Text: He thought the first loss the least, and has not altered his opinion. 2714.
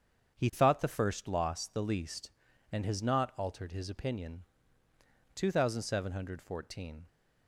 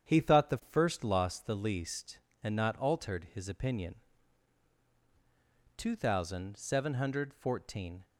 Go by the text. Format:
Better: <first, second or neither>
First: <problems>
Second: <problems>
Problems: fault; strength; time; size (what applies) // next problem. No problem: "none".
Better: first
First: starts louder than the rest; strong; until 1.3 s; 7.5 dB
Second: starts louder than the rest; strong; until 1.1 s; 8.5 dB // skips "has"; at 2.5 s